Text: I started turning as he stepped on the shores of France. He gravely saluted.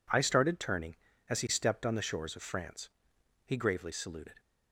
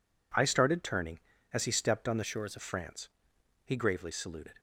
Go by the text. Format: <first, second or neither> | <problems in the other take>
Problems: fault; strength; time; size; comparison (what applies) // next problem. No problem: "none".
first | changes voice from "shores" to "of"; from 2.2 to 2.5 s; 0.3 s long